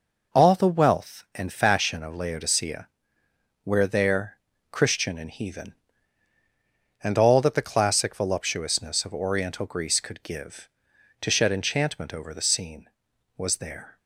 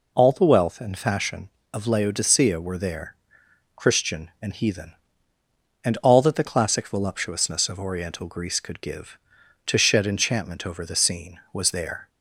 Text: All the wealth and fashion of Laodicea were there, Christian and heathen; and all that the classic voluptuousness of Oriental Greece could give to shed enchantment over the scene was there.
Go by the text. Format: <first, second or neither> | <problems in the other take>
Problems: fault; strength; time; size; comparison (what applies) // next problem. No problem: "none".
second | says "where" for "were"; at 3.6 s